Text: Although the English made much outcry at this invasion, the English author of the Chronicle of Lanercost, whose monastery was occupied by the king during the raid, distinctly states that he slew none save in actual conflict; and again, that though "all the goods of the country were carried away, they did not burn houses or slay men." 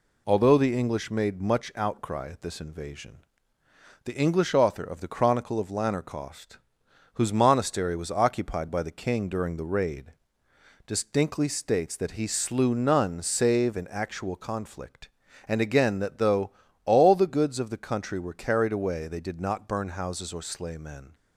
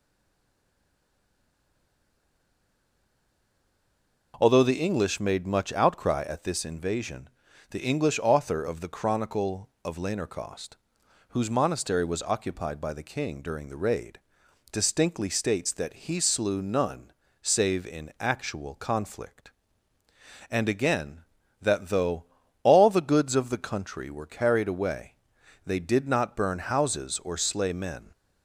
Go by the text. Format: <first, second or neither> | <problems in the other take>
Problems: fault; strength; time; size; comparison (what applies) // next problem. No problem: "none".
first | stays silent before the first word; strong; until 4.3 s; 4.3 s long // pauses between "none" and "save"; slight; at 17.1 s; 0.30 s long // pauses between "though" and "all"; at 22.2 s; 0.38 s long; slight in the first